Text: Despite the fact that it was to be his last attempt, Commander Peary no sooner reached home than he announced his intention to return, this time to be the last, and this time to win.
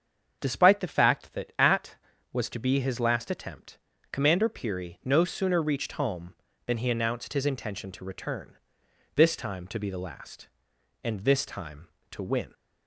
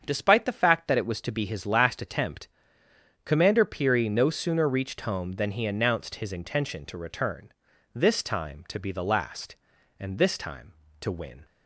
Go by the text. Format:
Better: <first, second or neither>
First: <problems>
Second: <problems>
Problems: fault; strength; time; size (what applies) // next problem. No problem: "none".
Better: second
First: starts louder than the rest; until 1.4 s; 7 dB // says "at" for "it"; at 1.5 s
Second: starts louder than the rest; until 1.0 s; 7 dB